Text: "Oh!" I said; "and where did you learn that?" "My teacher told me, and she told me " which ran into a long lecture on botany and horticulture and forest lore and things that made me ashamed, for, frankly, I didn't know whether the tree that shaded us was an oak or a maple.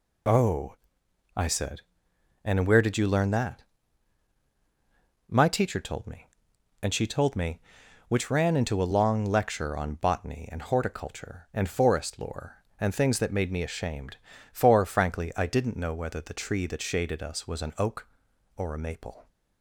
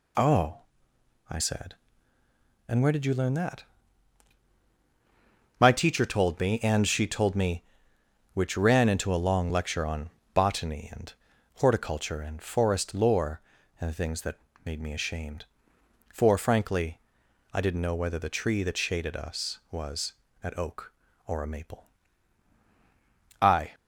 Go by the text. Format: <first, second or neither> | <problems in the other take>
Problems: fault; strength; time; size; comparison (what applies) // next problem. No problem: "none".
first | pauses between "on" and "botany"; slight; at 10.1 s; 0.22 s long // pauses between "and" and "horticulture"; at 11.1 s; 0.44 s long // pauses between "that" and "made"; slight; at 14.3 s; 0.26 s long // pauses between "was" and "an"; slight; at 20.1 s; 0.30 s long // goes on to say "I"; slight; from 23.4 s on; 0.34 s long